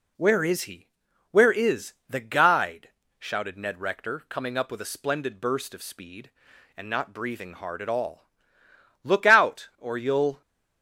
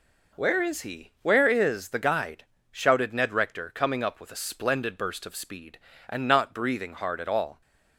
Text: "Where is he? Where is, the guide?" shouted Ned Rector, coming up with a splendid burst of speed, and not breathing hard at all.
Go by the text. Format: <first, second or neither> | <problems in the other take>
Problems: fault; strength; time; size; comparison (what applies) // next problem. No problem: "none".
second | goes on to say "Look out or you'll"; from 9.0 s on; 1.3 s long